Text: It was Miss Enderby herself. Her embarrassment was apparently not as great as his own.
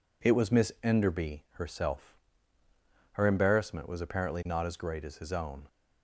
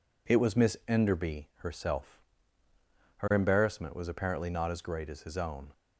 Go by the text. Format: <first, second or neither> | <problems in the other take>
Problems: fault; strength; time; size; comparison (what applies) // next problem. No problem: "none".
neither | none